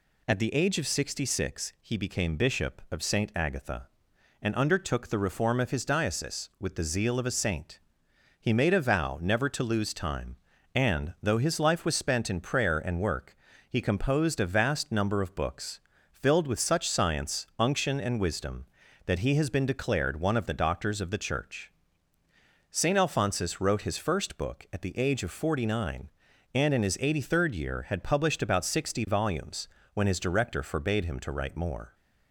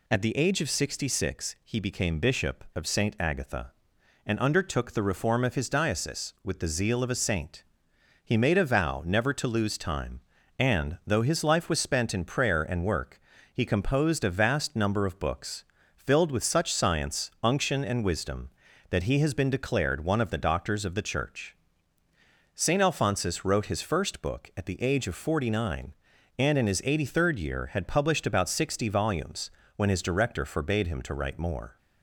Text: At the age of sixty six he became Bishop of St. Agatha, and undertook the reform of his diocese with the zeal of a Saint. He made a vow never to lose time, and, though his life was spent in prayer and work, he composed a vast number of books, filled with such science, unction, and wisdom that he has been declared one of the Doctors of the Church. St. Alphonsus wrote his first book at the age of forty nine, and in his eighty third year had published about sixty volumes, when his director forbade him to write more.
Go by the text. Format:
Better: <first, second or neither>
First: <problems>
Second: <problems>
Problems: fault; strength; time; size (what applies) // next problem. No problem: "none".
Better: neither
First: none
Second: none